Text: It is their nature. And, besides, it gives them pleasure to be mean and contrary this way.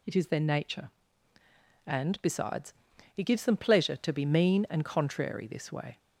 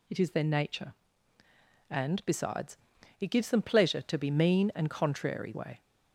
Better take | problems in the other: first | skips "this"; at 5.5 s

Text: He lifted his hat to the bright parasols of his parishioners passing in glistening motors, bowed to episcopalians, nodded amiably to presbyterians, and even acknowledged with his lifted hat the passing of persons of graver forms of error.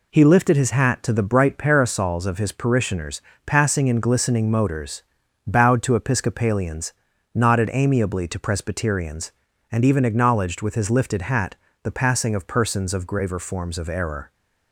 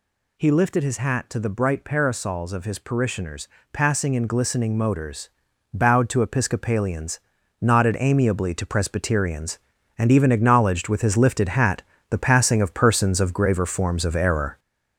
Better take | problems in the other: first | gets louder; noticeable; throughout; 5.5 dB // pauses between "parishioners" and "passing"; slight; at 3.4 s; 0.24 s long; slight in the first // pauses between "hat" and "the"; slight; at 11.8 s; 0.30 s long; slight in the first

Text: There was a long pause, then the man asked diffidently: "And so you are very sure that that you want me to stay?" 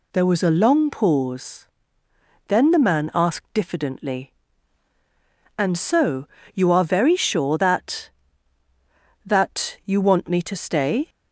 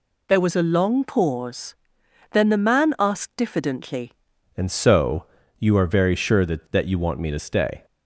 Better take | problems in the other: first | changes voice at "And"; from 4.5 s on; 3.3 s long // pauses between "so" and "you"; slight; at 5.2 s; 0.34 s long; slight in the first

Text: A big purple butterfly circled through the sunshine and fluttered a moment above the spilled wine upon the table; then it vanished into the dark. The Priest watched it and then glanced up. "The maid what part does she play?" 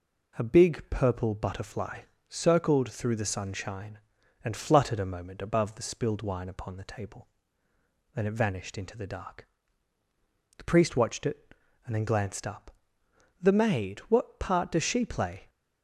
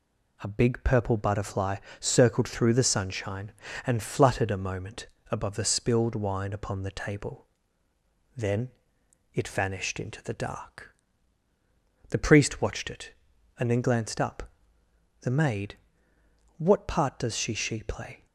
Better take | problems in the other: first | pauses between "butterfly" and "circled"; slight; at 1.7 s; 0.22 s long; slight in the first // pauses between "moment" and "above"; slight; at 5.0 s; 0.22 s long // pauses between "then" and "it"; noticeable; at 8.6 s; 0.62 s long // pauses between "maid" and "what"; noticeable; at 15.7 s; 0.80 s long // says "she" twice; at 17.5 s

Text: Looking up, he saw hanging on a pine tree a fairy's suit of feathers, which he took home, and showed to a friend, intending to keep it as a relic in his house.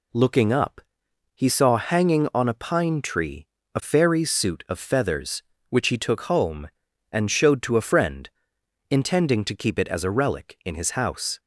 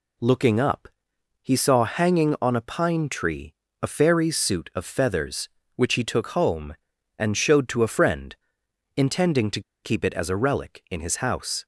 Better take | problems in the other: first | pauses between "tree" and "a"; slight; at 3.5 s; 0.30 s long; slight in the first // pauses between "to" and "keep"; slight; at 9.6 s; 0.21 s long

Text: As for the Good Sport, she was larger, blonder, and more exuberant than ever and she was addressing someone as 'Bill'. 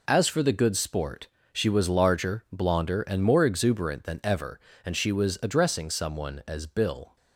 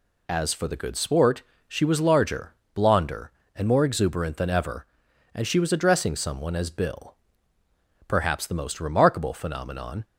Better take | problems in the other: first | goes on to say "Perhaps the most remarkable phenomenon"; strong; from 8.0 s on; 1.9 s long

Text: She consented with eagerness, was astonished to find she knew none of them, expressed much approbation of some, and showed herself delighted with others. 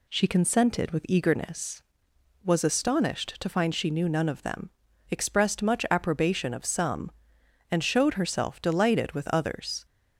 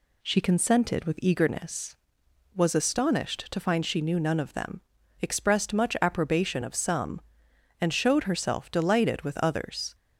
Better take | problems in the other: neither | none

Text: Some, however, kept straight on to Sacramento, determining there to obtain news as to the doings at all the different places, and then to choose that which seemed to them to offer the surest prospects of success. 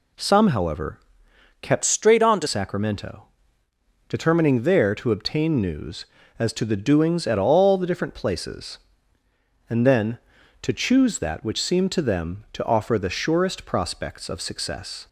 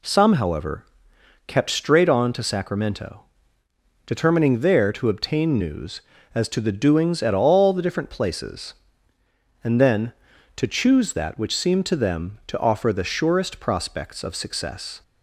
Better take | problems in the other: second | changes voice from "straight" to "to"; from 1.8 to 2.4 s; 0.6 s long

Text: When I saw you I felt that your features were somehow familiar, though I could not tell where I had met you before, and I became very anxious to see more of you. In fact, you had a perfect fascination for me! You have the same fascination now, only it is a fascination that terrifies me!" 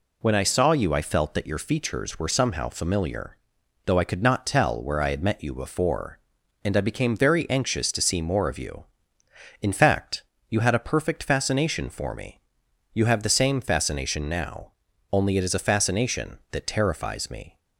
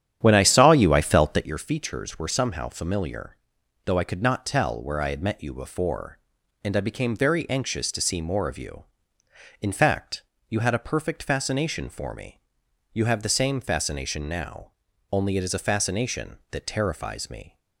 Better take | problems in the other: first | starts louder than the rest; strong; until 1.6 s; 10 dB

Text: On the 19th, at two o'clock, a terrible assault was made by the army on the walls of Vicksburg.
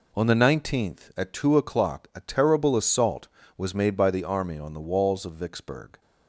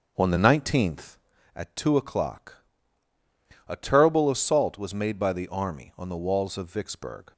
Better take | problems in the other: first | starts louder than the rest; until 1.3 s; 7 dB

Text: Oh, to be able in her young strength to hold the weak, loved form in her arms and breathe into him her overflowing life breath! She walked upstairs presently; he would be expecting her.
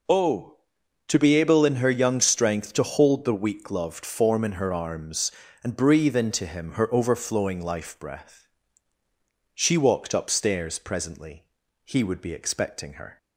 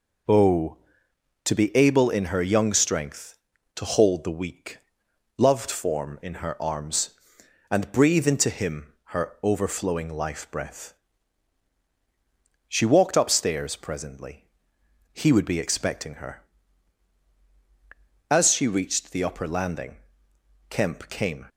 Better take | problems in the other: first | goes on to say "As she reached the upper landing Kemp came"; strong; from 18.3 s on; 3.1 s long

